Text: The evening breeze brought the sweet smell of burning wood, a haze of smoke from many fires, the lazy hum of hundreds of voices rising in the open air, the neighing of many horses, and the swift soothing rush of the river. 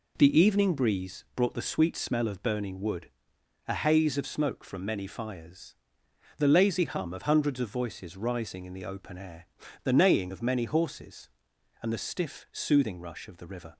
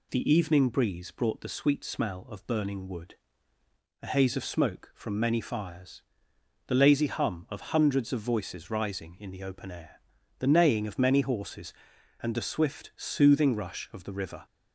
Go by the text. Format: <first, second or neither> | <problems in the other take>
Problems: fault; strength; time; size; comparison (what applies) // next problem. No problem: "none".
second | says "stiff" for "swift"; at 11.9 s